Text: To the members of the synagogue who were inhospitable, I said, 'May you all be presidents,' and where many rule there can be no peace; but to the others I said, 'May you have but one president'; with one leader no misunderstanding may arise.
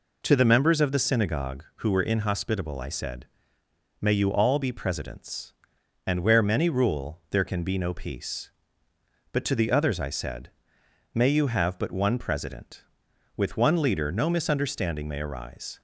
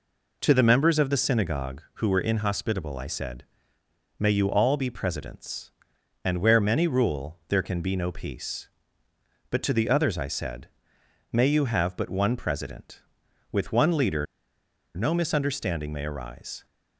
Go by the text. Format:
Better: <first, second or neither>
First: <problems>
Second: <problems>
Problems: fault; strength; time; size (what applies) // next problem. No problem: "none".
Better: first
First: none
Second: pauses between "leader" and "no"; noticeable; at 14.2 s; 0.71 s long